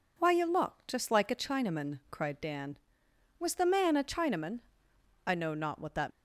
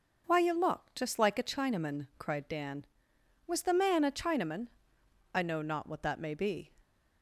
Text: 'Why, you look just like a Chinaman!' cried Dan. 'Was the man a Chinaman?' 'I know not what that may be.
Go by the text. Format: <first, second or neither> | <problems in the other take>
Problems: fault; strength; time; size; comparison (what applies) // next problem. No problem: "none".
second | stops before "may be"; at 6.1 s